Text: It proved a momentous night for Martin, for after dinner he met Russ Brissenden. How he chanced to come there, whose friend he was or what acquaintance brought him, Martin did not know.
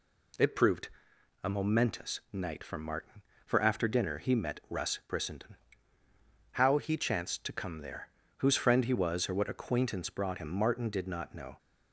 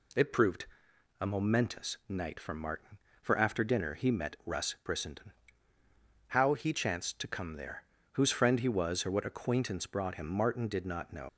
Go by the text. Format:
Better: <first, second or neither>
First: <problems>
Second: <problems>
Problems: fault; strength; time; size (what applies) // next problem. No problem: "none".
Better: first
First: pauses between "proved" and "a"; noticeable; at 0.8 s; 0.54 s long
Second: pauses between "proved" and "a"; noticeable; at 0.6 s; 0.54 s long // leaves "know" unfinished; at 11.2 s; 70 ms